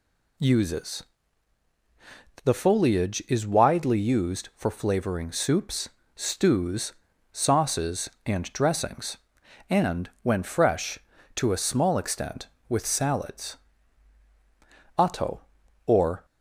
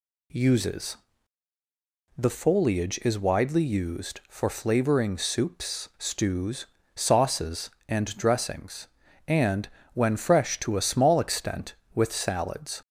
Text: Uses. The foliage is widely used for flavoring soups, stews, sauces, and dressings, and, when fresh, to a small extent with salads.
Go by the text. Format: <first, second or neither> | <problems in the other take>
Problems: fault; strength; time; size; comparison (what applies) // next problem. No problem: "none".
second | goes on to say "Otto or"; noticeable; from 14.9 s on; 1.2 s long